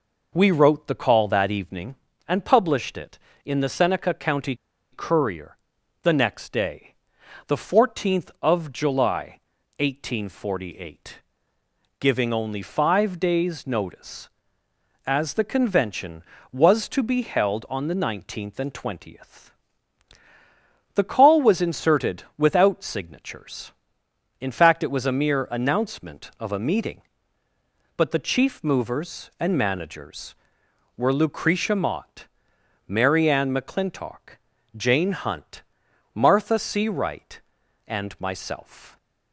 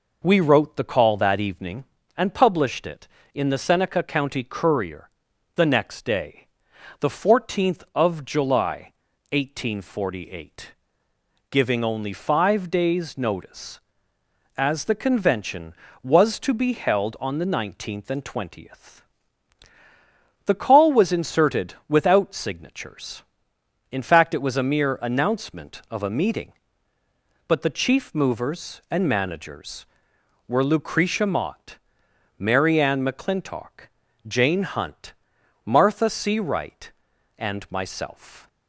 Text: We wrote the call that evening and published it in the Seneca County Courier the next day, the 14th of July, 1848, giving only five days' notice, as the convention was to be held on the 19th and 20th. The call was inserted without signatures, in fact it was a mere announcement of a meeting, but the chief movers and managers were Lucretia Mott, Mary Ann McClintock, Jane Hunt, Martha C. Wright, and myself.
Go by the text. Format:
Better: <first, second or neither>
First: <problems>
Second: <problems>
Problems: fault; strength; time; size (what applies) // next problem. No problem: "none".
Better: second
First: pauses between "County" and "Courier"; at 4.5 s; 0.36 s long // pauses between "Courier" and "the"; noticeable; at 5.5 s; 0.46 s long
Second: pauses between "Courier" and "the"; noticeable; at 5.0 s; 0.46 s long